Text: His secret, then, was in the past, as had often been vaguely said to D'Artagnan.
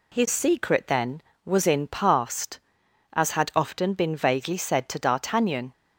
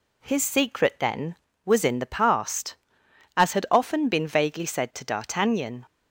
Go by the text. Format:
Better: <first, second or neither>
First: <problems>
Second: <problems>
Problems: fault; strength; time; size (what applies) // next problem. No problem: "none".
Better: second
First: skips "the"; at 1.8 s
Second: none